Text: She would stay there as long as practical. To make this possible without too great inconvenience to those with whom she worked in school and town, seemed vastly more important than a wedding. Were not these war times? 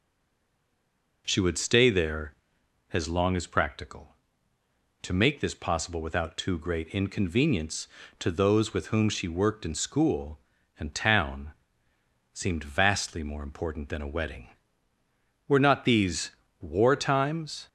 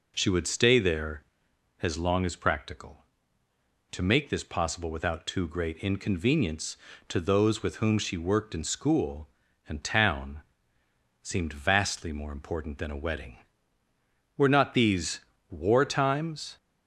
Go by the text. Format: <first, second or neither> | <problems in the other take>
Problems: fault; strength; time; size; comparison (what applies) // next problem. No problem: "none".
second | stays silent before the first word; noticeable; until 1.2 s; 1.2 s long // pauses between "these" and "war"; slight; at 16.3 s; 0.28 s long; slight in the second